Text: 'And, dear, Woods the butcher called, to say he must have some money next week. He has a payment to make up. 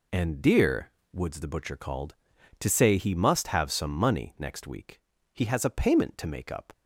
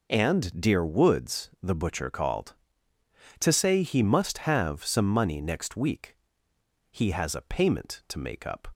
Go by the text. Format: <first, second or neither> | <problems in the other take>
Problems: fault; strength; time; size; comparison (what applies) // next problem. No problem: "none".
neither | none